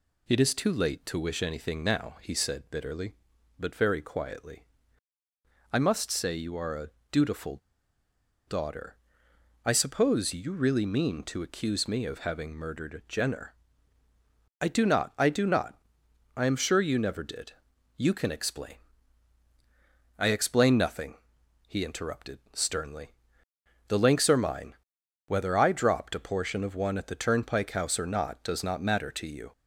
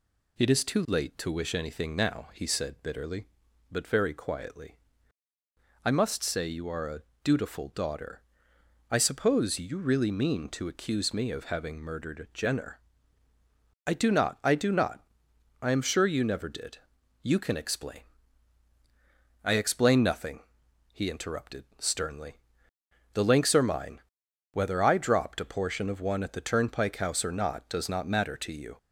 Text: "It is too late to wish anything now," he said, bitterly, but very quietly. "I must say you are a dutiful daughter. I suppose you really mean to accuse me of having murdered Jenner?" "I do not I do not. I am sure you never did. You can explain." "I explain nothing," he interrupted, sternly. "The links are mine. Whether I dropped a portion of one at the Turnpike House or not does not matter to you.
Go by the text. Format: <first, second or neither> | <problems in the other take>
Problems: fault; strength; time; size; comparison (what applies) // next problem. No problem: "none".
second | pauses between "a" and "dutiful"; slight; at 6.8 s; 0.22 s long; slight in the second // pauses between "dutiful" and "daughter"; noticeable; at 7.5 s; 0.89 s long